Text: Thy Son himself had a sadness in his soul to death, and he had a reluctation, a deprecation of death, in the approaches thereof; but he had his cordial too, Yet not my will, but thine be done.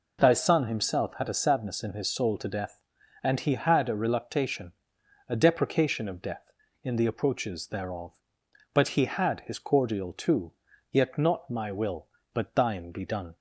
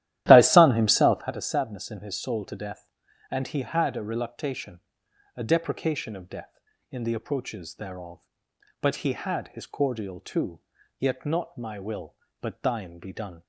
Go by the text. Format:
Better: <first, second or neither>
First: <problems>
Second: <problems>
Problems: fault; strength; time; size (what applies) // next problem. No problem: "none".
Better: first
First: none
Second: starts louder than the rest; strong; until 1.4 s; 13.5 dB